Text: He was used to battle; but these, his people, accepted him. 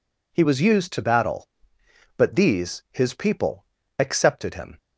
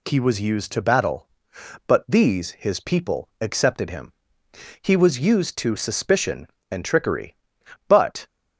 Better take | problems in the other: first | goes on to say "He was used to suspicion and trickery but"; strong; from 4.8 s on; 3.4 s long

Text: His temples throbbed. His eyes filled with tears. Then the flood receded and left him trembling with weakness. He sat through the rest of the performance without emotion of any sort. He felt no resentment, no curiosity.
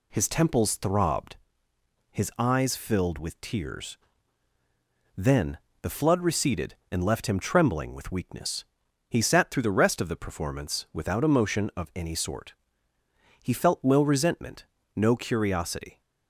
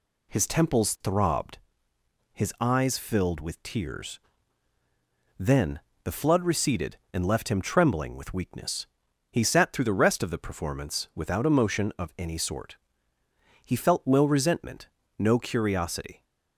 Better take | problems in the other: neither | pauses between "Then" and "the"; slight; the same in both

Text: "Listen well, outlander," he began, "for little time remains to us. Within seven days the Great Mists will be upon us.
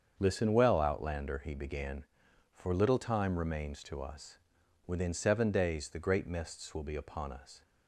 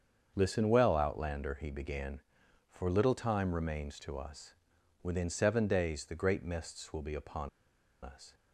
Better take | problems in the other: first | starts louder than the rest; until 1.3 s; 7 dB; also in the first // pauses between "upon" and "us"; noticeable; at 7.4 s; 0.54 s long

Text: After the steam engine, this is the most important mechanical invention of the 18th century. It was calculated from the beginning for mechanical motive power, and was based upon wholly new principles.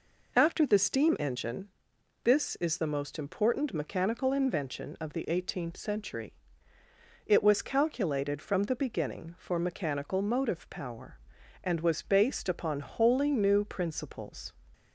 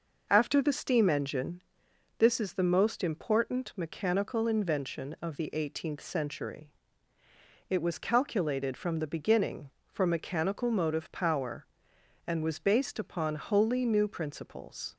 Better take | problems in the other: neither | none

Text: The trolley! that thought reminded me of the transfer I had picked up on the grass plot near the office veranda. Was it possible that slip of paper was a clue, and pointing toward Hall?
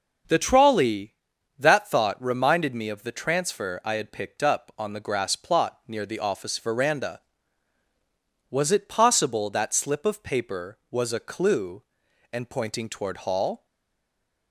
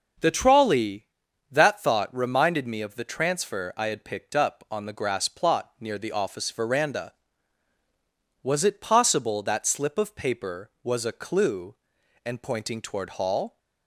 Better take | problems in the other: second | starts louder than the rest; until 1.7 s; 6.5 dB; also in the second // stays silent after the last word; slight; from 13.6 s on; 0.9 s long

